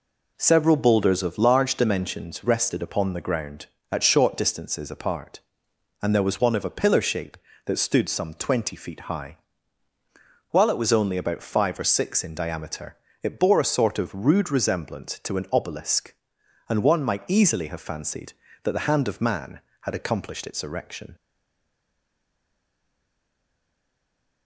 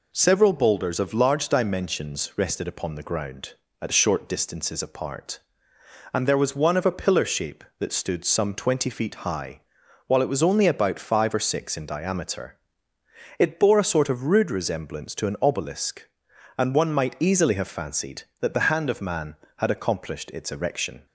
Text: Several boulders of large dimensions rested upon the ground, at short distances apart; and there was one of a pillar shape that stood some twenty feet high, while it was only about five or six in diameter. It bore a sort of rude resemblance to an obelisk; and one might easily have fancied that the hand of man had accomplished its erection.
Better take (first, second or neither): second